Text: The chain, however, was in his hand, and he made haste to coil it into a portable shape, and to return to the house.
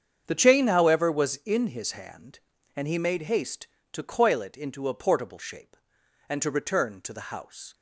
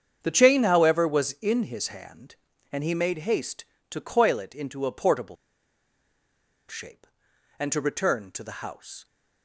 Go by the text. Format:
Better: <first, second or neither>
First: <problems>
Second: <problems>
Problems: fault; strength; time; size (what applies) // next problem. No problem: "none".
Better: first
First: starts louder than the rest; strong; until 1.2 s; 7.5 dB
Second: starts louder than the rest; strong; until 1.2 s; 7.5 dB // pauses between "portable" and "shape"; strong; at 5.3 s; 1.3 s long